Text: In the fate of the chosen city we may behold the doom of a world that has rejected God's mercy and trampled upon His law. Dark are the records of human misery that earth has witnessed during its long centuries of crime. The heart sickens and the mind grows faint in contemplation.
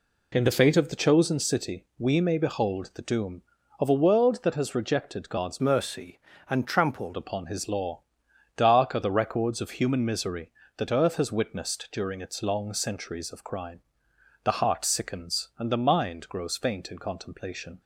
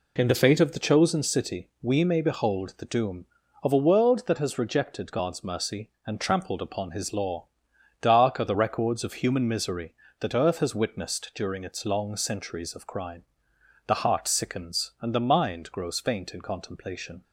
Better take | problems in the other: second | changes voice from "mercy" to "trampled"; from 5.6 to 7.1 s; 1.5 s long

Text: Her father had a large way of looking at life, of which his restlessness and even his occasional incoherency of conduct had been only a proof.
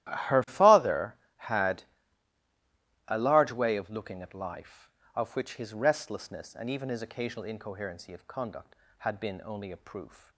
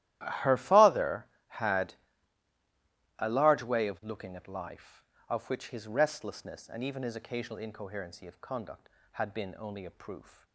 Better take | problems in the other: neither | starts louder than the rest; strong; the same in both // pauses between "had" and "a"; the same in both

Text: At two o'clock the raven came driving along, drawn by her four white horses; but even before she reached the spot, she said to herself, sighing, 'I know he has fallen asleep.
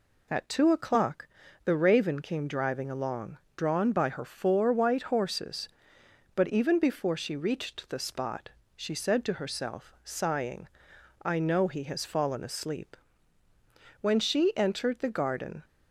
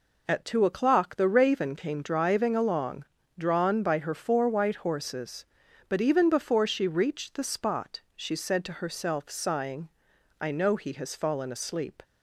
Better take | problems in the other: second | pauses between "o'clock" and "the"; slight; at 1.2 s; 0.36 s long // goes on to say "When she entered the garden"; from 13.9 s on; 1.6 s long

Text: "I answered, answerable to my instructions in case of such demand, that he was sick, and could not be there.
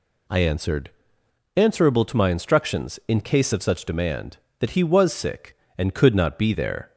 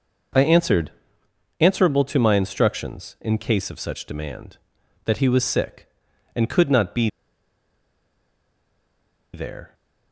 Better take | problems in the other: first | pauses between "be" and "there"; strong; at 7.0 s; 2.2 s long

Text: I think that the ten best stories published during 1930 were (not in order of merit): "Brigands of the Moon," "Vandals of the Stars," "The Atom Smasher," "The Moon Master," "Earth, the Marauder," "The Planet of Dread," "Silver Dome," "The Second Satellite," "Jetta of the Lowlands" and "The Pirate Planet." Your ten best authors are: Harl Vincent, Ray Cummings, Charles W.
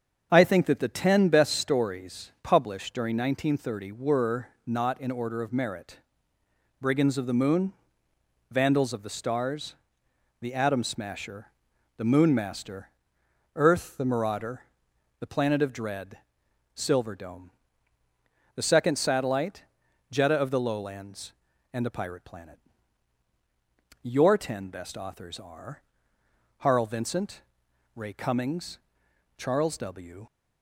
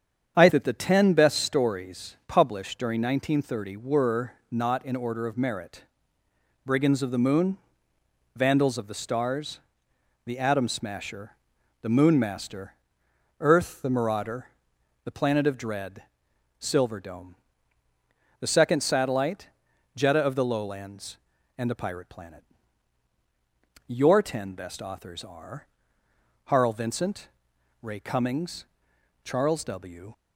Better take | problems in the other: first | starts louder than the rest; strong; until 1.3 s; 8 dB; also in the first // skips "think"; at 0.4 s

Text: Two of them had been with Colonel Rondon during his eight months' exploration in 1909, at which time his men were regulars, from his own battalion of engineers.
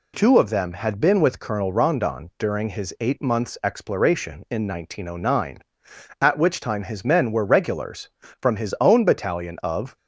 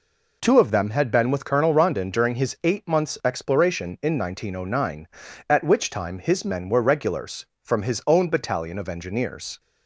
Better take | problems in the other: second | stops before "engineers"; at 9.9 s

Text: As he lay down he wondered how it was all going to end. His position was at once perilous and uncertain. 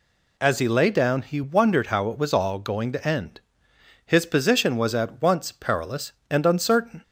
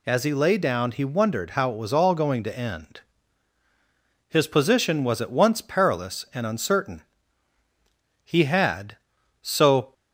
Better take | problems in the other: first | goes on to say "He had so"; strong; from 8.2 s on; 1.7 s long

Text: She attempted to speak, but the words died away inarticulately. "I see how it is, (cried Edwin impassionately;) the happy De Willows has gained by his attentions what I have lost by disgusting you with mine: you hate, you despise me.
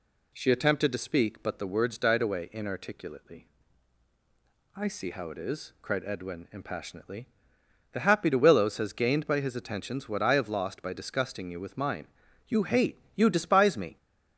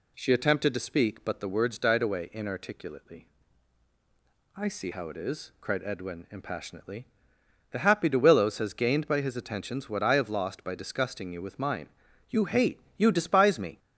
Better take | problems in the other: neither | none

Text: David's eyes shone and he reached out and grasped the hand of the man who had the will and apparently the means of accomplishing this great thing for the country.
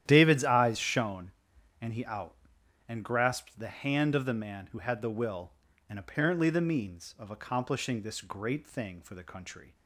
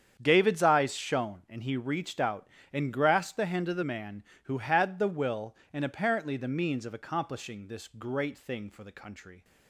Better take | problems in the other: second | starts louder than the rest; strong; until 1.0 s; 11 dB; strong in the second // skips "reached"; at 2.0 s

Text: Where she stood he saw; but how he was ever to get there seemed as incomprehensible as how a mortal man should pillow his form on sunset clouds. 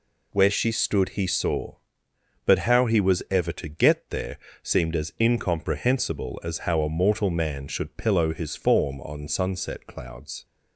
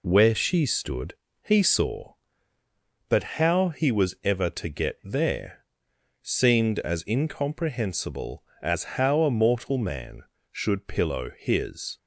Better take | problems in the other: first | pauses between "stood" and "he"; slight; at 1.1 s; 0.26 s long // pauses between "there" and "seemed"; noticeable; at 5.6 s; 0.56 s long; slight in the first // stops before "form on sunset clouds"; at 11.9 s

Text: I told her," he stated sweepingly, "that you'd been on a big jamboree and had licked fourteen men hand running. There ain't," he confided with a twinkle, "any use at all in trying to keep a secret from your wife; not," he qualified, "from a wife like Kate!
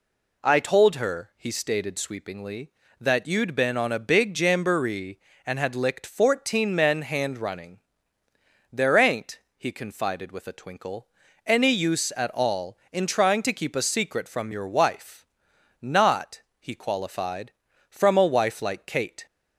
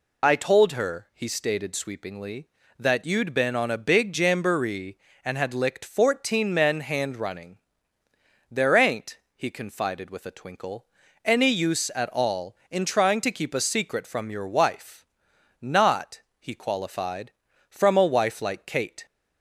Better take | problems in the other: first | loses the start of "I"; at 0.2 s; 55 ms

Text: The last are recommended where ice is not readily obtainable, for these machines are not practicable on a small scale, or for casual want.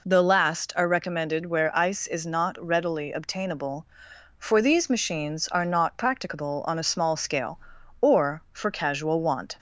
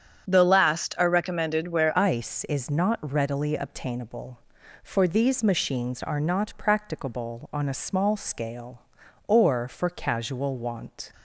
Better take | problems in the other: first | starts louder than the rest; strong; until 1.3 s; 8.5 dB // changes voice at "ice"; from 1.9 s on; 9.2 s long

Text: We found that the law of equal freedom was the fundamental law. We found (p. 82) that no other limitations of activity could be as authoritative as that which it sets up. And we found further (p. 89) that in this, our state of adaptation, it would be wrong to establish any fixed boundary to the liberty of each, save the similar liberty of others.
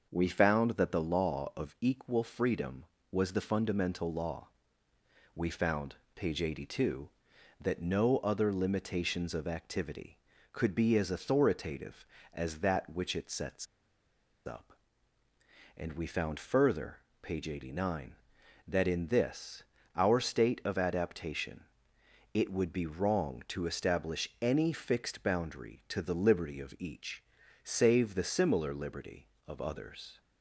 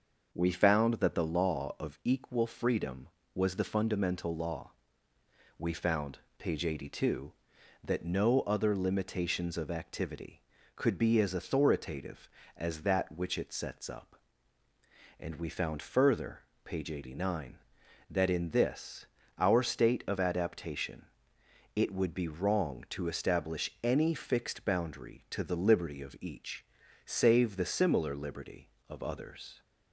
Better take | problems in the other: second | starts louder than the rest; noticeable; until 1.1 s; 6 dB; noticeable in the second // pauses between "sets" and "up"; noticeable; at 13.6 s; 0.80 s long

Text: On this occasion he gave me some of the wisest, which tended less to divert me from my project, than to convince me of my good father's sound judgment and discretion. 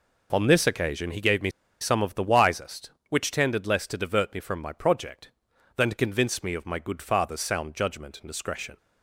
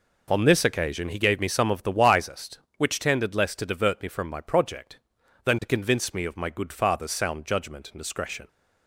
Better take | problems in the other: second | pauses between "me" and "some"; slight; at 1.4 s; 0.31 s long

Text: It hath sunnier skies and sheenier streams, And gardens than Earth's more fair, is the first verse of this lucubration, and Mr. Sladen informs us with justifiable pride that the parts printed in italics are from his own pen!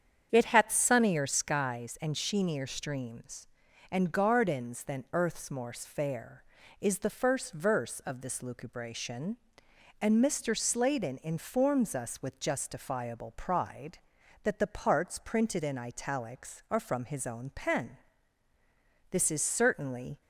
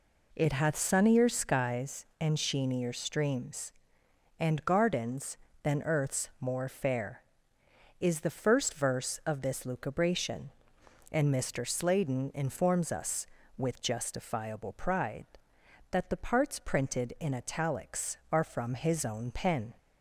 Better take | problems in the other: second | starts louder than the rest; strong; until 1.3 s; 8 dB // goes on to say "This is certainly"; noticeable; from 19.1 s on; 1.1 s long

